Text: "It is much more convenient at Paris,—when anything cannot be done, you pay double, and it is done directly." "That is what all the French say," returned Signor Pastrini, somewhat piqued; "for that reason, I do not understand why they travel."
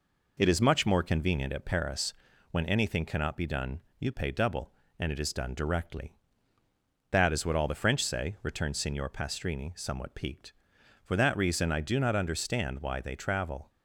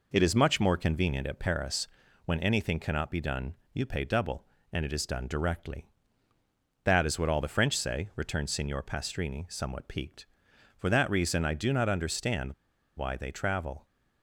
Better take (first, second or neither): first